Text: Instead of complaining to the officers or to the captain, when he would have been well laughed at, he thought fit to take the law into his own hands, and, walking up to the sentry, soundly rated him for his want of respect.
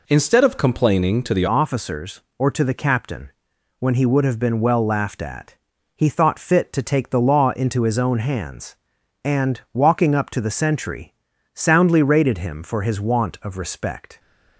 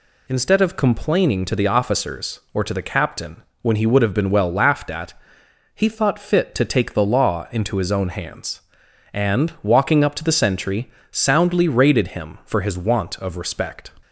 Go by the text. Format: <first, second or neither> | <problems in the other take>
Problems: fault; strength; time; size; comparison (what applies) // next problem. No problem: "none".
second | changes voice at "officers"; from 1.4 s on; 12.7 s long